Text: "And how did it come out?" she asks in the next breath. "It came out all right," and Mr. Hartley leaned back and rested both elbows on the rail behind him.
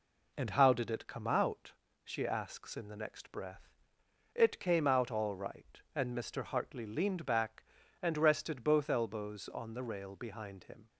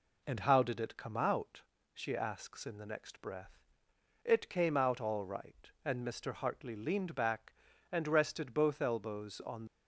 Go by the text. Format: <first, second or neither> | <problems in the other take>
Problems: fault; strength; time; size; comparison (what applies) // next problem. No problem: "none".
first | stops before "the rail behind him"; at 9.6 s